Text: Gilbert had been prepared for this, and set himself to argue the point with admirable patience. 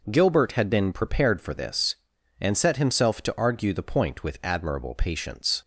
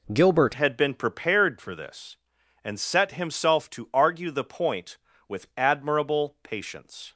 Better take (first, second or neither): first